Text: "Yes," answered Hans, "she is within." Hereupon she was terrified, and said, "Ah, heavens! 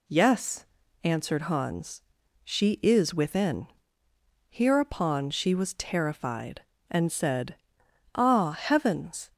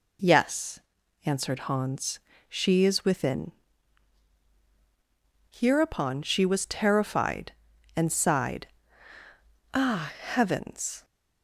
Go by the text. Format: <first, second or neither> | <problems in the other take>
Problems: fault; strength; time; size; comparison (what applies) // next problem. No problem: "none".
first | says "sighed" for "said"; at 8.1 s